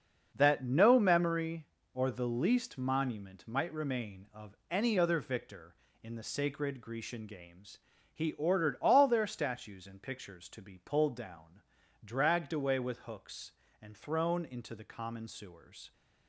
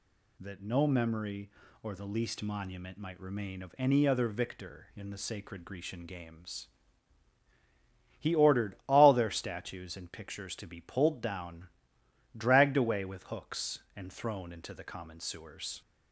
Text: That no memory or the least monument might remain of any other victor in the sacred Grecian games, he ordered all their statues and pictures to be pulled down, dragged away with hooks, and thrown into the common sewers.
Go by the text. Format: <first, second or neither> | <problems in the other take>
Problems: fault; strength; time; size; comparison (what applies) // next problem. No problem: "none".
second | gets quieter; strong; throughout; 9.5 dB // pauses between "of" and "any"; slight; at 4.5 s; 0.16 s long